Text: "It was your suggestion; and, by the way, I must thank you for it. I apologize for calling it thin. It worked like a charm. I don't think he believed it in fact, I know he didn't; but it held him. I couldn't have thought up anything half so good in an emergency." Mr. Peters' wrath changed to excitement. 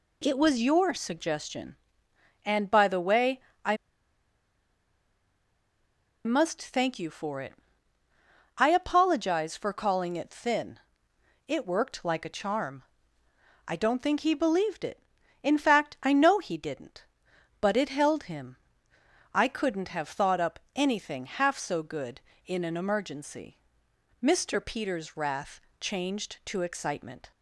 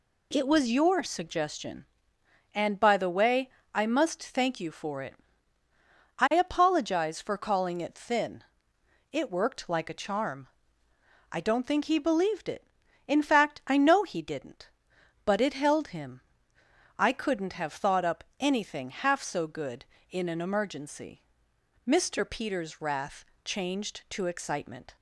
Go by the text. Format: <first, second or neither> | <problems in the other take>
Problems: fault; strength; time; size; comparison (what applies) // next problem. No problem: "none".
second | pauses between "I" and "must"; strong; at 3.7 s; 2.4 s long // pauses between "wrath" and "changed"; slight; at 25.5 s; 0.22 s long; slight in the second